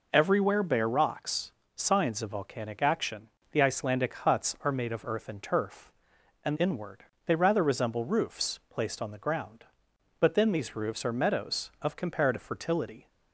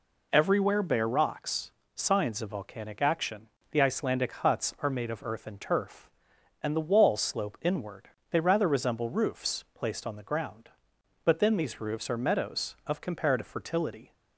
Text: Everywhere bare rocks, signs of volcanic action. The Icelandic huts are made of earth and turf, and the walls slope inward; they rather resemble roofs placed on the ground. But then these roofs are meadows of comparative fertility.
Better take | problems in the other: second | skips "the walls slope"; at 6.5 s

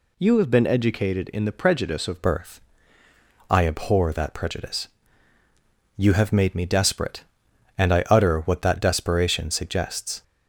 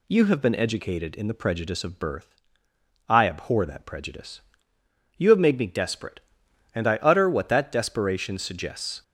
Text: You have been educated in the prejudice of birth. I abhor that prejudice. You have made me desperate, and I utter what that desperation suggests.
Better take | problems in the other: second | changes voice at "birth"; from 2.2 s on; 8.0 s long

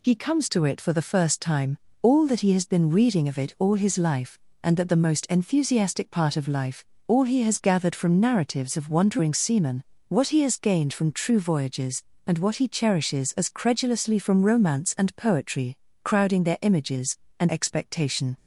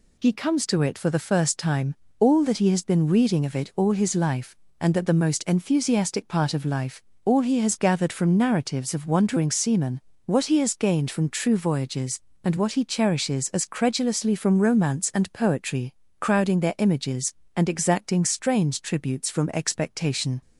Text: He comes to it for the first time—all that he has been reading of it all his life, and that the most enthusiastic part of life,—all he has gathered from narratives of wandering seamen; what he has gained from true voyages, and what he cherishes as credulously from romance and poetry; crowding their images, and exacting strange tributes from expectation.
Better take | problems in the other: second | skips "exacting strange tributes from"; at 17.4 s

